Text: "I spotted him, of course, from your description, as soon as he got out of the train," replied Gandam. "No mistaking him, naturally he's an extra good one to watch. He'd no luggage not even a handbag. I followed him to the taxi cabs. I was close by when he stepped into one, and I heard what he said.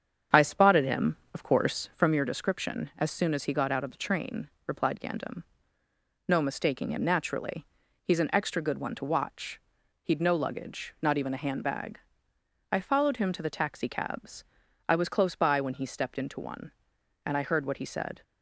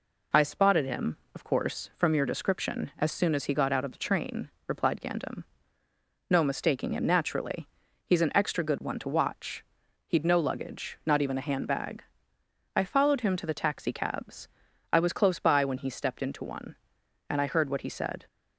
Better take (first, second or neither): second